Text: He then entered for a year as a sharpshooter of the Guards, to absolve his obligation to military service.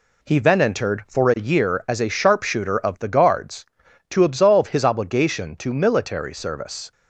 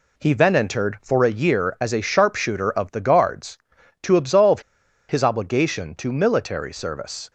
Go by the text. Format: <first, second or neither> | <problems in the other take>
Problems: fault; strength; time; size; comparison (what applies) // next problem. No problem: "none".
first | pauses between "absolve" and "his"; noticeable; at 4.5 s; 0.49 s long